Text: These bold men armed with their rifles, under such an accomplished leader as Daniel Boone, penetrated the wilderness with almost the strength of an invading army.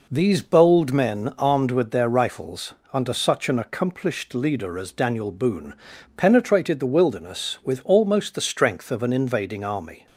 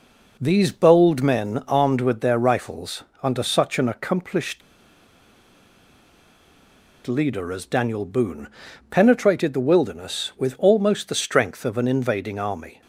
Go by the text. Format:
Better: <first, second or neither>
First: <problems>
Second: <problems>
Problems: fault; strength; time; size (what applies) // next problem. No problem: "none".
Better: first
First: none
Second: pauses between "accomplished" and "leader"; strong; at 4.6 s; 2.4 s long